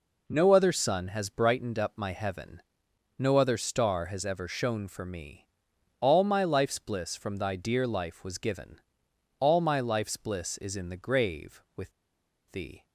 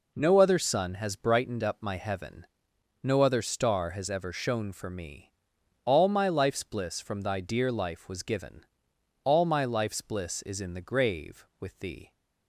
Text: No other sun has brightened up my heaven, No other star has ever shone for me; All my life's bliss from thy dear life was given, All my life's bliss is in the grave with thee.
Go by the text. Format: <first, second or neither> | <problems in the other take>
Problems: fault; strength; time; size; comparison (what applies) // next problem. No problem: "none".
second | pauses between "with" and "thee"; noticeable; at 11.9 s; 0.61 s long